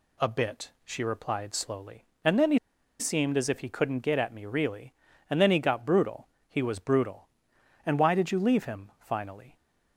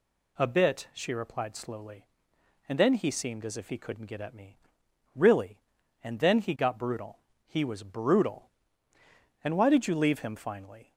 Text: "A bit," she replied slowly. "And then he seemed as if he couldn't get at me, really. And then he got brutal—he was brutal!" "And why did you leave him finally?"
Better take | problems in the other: second | pauses between "he" and "seemed"; at 2.5 s; 0.40 s long

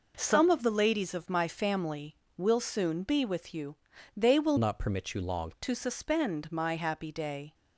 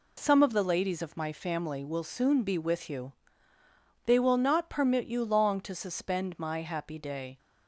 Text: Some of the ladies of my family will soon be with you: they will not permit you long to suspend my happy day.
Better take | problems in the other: second | changes voice from "not" to "long"; from 4.5 to 5.5 s; 1.0 s long

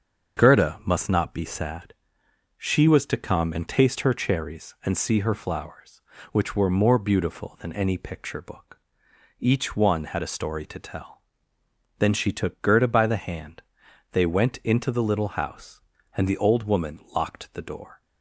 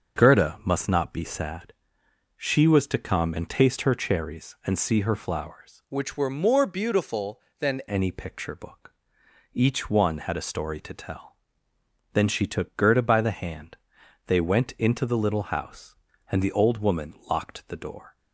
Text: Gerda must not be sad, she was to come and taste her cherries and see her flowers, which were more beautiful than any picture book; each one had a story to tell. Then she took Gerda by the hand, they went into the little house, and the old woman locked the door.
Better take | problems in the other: first | starts louder than the rest; until 1.2 s; 6.5 dB; also in the first // changes voice from "which" to "than"; from 5.8 to 7.7 s; 1.9 s long

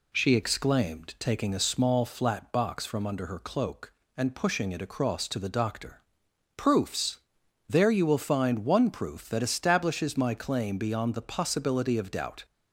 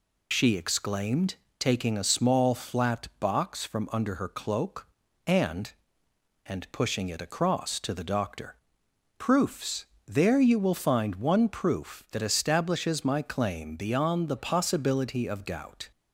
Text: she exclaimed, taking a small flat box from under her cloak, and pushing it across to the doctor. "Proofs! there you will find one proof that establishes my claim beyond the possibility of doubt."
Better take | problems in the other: first | says "and" twice; at 6.4 s

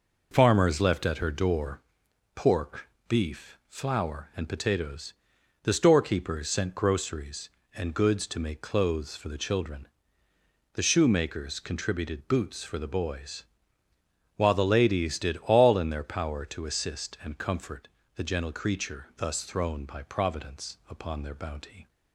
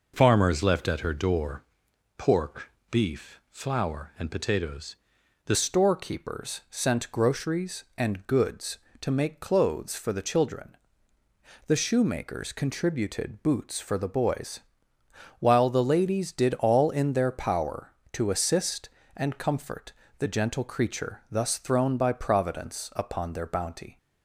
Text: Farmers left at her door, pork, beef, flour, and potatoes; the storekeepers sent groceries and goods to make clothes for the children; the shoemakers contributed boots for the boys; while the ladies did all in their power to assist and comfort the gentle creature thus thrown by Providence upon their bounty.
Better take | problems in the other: first | changes voice at "storekeepers"; from 5.5 s on; 18.4 s long // pauses between "comfort" and "the"; slight; at 19.9 s; 0.28 s long; slight in the first

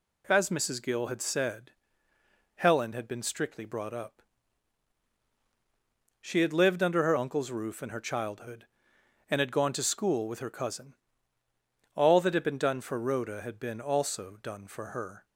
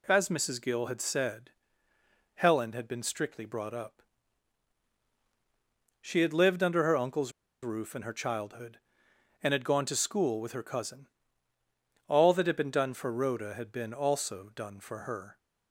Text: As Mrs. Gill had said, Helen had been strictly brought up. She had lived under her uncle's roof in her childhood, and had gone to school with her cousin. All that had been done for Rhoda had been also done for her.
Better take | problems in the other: first | pauses between "uncle's" and "roof"; slight; at 7.3 s; 0.31 s long

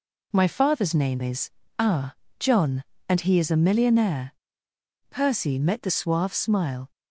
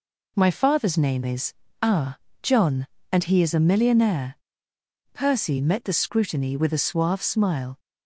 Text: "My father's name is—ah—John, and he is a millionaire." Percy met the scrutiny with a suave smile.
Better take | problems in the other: second | skips "scrutiny with a"; at 5.8 s

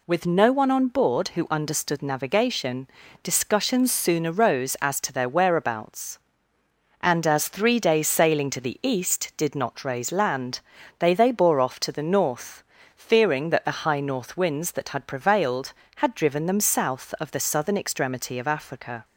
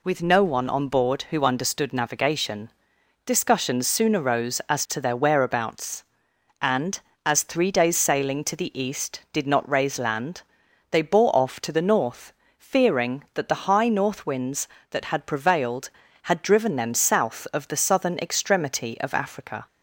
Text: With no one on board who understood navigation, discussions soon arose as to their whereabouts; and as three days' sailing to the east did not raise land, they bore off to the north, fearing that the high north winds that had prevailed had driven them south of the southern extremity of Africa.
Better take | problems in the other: second | says "they" twice; at 11.1 s

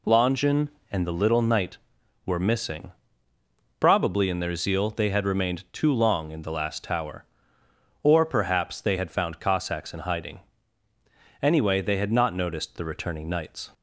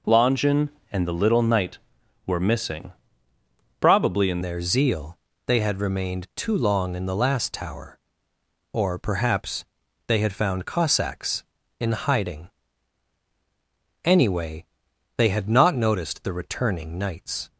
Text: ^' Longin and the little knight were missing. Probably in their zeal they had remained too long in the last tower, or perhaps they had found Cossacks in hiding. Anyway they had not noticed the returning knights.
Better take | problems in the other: first | changes voice at "their"; from 4.4 s on; 13.0 s long // pauses between "zeal" and "they"; slight; at 5.1 s; 0.28 s long // pauses between "perhaps" and "they"; at 9.6 s; 0.44 s long // pauses between "Anyway" and "they"; noticeable; at 14.6 s; 0.50 s long

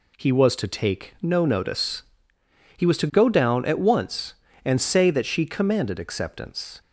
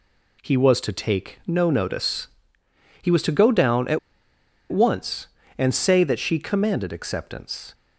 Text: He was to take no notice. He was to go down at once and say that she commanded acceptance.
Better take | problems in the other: first | pauses between "at" and "once"; noticeable; at 3.9 s; 0.72 s long

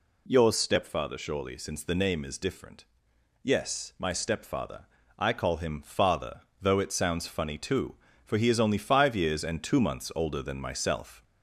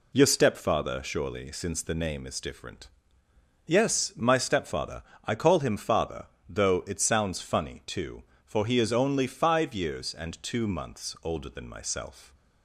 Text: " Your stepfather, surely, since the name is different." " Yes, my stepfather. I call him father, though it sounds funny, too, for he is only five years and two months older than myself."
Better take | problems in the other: second | gets louder; noticeable; throughout; 4 dB

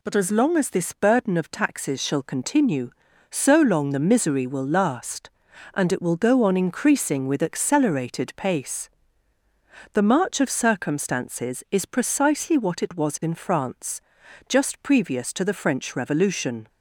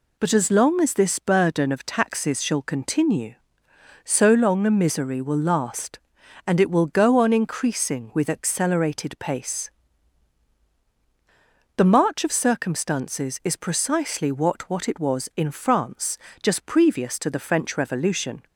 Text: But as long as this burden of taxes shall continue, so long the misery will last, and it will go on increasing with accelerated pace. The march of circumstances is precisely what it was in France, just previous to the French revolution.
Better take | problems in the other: first | says "what" twice; at 14.6 s

